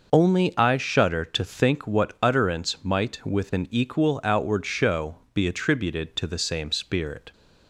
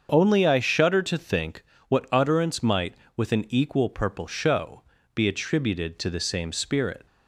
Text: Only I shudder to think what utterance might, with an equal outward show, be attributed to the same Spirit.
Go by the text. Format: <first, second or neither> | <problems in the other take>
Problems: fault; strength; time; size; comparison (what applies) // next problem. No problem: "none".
first | starts louder than the rest; until 1.1 s; 7 dB; noticeable in the first // pauses between "think" and "what"; slight; at 1.6 s; 0.24 s long // says "purple" for "outward"; at 3.8 s